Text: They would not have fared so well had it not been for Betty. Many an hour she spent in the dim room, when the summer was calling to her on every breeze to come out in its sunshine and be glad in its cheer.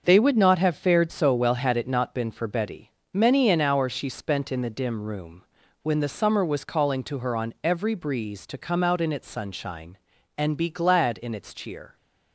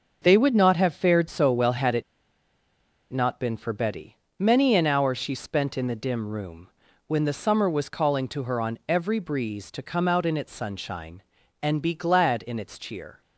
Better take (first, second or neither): first